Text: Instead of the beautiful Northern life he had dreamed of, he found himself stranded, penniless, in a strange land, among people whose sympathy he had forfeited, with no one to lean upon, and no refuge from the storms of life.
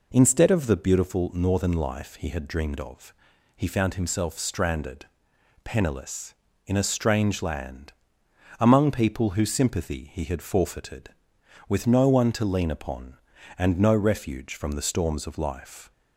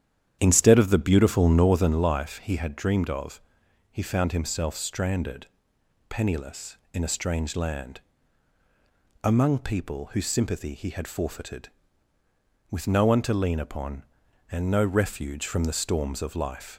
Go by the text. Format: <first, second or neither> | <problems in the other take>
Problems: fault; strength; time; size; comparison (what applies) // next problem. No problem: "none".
first | starts louder than the rest; strong; until 2.1 s; 10 dB